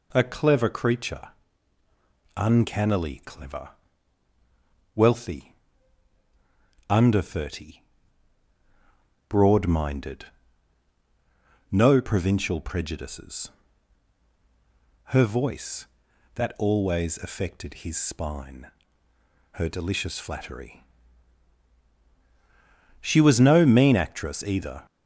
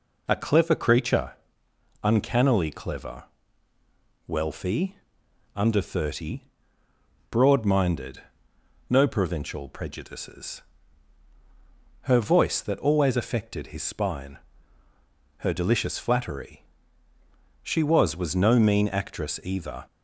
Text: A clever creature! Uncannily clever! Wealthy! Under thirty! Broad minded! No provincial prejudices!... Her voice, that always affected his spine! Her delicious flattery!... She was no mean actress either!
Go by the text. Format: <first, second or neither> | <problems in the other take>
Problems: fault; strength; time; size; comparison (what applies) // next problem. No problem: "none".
first | says "was" twice; at 18.1 s